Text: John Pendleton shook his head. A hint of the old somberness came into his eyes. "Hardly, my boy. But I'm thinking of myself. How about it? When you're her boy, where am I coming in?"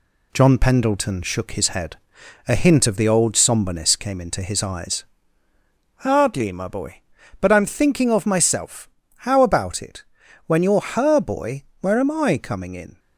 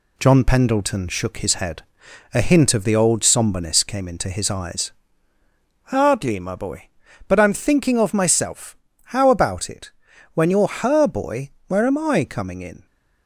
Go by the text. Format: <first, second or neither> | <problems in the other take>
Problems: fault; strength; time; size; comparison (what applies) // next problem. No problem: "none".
neither | none